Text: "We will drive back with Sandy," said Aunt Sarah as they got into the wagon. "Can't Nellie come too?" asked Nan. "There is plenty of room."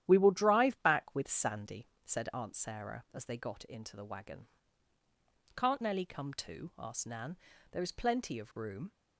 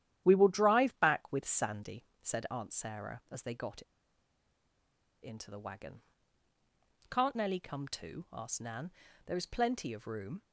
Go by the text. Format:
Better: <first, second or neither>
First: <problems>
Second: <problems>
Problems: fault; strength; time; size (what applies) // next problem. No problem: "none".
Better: first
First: starts louder than the rest; strong; until 1.0 s; 11.5 dB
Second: starts louder than the rest; strong; until 1.2 s; 11.5 dB // pauses between "got" and "into"; strong; at 3.8 s; 1.3 s long